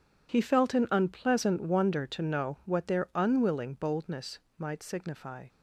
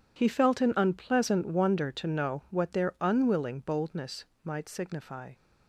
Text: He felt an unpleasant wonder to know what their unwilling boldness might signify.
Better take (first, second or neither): neither